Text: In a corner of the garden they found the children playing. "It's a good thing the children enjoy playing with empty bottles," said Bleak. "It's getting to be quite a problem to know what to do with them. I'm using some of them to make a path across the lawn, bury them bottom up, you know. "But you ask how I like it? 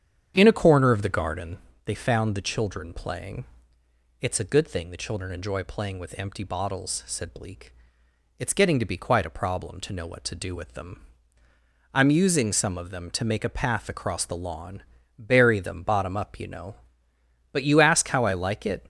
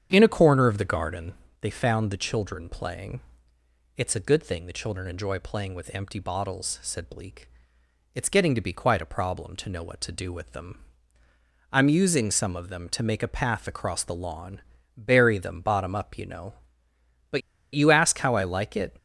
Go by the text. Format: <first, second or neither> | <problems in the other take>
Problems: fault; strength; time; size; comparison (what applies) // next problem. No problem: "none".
first | starts louder than the rest; strong; until 1.1 s; 8.5 dB; strong in the first // pauses between "garden" and "they"; slight; at 1.3 s; 0.26 s long; slight in the first // pauses between "But" and "you"; slight; at 17.4 s; 0.32 s long